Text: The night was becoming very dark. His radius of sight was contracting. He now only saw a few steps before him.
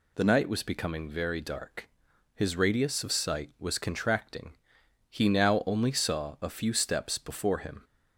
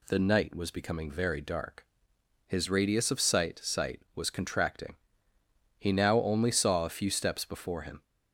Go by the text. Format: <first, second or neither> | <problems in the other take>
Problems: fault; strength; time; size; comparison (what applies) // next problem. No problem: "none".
first | says "sight" twice; at 3.6 s